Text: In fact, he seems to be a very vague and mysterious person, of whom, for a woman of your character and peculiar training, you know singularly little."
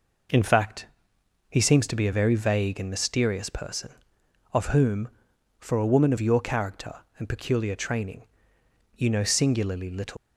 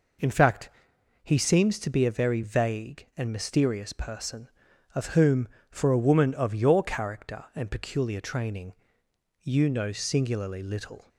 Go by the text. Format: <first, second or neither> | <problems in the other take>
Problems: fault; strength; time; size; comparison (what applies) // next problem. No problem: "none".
second | leaves "little" unfinished; at 10.1 s; 160 ms